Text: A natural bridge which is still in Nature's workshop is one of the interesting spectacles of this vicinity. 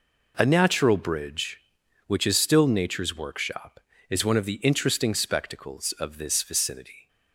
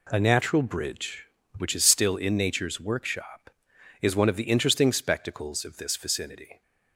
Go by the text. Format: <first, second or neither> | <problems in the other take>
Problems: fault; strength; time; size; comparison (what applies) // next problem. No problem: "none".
second | skips "in"; at 2.6 s